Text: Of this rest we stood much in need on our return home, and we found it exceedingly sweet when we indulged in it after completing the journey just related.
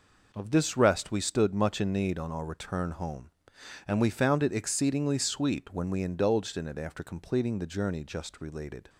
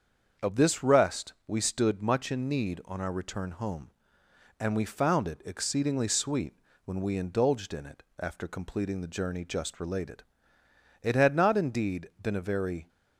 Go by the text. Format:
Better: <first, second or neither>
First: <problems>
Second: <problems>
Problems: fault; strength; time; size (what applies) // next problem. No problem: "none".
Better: first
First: none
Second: starts louder than the rest; until 1.5 s; 7 dB // pauses between "sweet" and "when"; slight; at 6.5 s; 0.30 s long // pauses between "it" and "after"; slight; at 8.0 s; 0.18 s long // goes on to say "It had not indeed been a very"; strong; from 11.0 s on; 1.8 s long